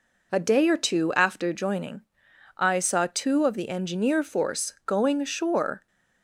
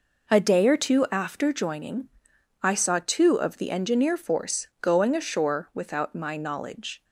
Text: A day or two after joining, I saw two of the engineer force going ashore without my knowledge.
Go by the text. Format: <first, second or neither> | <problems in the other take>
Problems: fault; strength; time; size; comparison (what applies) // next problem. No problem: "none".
second | stops before "without my knowledge"; at 5.8 s